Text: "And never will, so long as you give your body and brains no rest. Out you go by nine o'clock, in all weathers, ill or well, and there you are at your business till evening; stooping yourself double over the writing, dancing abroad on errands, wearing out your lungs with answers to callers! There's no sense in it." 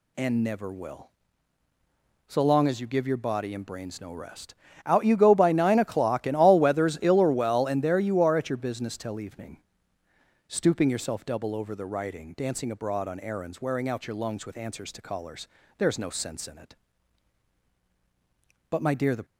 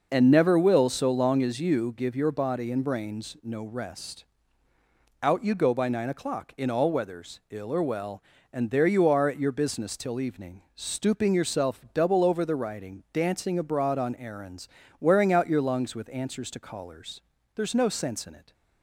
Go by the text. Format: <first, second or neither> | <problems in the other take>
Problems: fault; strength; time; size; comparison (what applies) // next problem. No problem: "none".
second | goes on to say "But my dear the"; from 18.7 s on; 0.54 s long